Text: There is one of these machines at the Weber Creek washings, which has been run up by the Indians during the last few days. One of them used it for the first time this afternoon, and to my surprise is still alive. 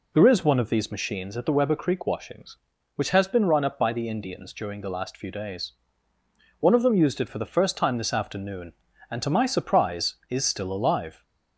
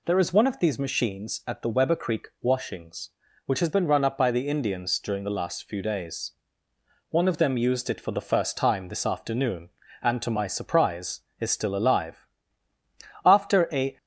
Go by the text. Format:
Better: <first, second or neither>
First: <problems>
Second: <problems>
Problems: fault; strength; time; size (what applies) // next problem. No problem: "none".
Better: first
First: none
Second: goes on to say "After a"; noticeable; from 13.2 s on; 0.72 s long